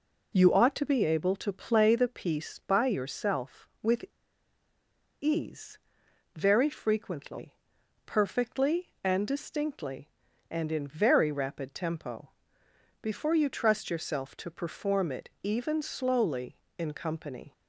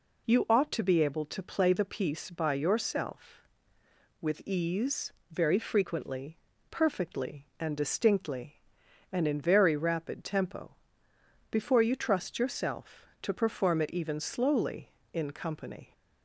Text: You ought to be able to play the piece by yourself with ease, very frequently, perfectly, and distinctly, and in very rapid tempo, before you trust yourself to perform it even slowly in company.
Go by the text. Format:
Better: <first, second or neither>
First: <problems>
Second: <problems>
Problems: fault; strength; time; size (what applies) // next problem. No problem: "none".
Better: second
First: pauses between "with" and "ease"; at 4.0 s; 1.1 s long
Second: none